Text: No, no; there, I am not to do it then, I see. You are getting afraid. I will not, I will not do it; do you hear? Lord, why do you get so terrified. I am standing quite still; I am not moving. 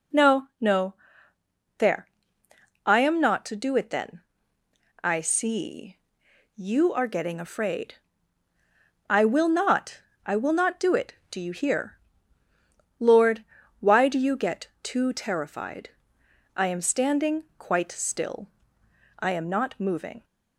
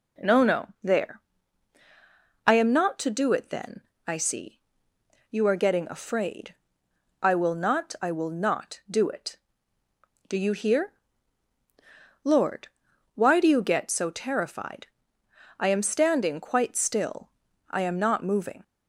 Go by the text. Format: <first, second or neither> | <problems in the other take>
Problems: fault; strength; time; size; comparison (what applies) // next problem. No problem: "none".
second | says "too" for "so"; at 14.8 s